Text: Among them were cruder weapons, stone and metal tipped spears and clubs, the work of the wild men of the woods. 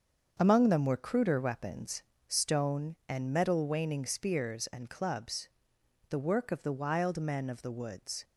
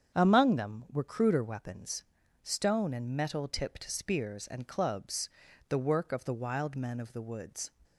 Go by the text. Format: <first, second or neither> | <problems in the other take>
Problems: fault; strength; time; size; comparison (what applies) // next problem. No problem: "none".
second | starts louder than the rest; until 1.4 s; 7 dB; strong in the second // says "waning" for "tipped"; at 3.6 s